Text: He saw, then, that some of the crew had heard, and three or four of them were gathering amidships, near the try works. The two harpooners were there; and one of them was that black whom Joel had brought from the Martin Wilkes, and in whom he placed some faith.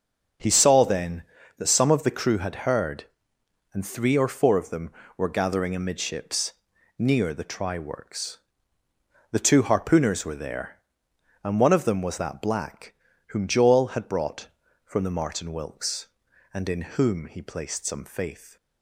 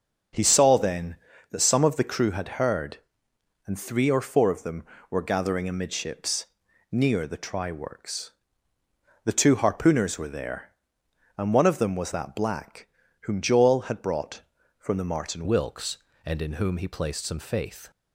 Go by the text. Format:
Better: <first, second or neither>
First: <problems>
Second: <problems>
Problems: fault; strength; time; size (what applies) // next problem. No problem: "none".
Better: first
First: starts louder than the rest; until 1.7 s; 6.5 dB // pauses between "black" and "whom"; slight; at 12.9 s; 0.34 s long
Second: starts louder than the rest; until 1.7 s; 6.5 dB // pauses between "black" and "whom"; slight; at 12.8 s; 0.34 s long // changes voice at "Wilkes"; from 15.4 s on; 2.5 s long